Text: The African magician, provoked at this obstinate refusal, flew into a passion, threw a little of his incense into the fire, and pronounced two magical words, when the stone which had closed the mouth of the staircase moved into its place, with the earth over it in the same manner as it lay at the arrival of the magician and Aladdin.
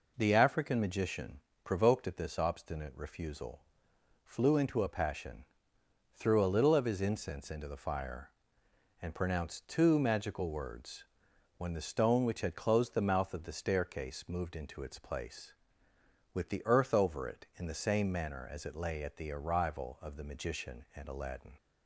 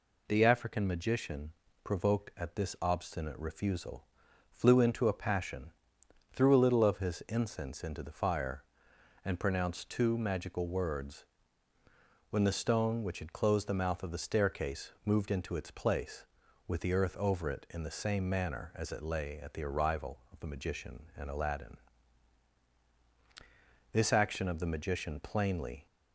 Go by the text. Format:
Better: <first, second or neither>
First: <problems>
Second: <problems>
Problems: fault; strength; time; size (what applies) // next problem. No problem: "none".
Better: first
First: none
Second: goes on to say "This action of the magician plainly"; strong; from 23.9 s on; 1.9 s long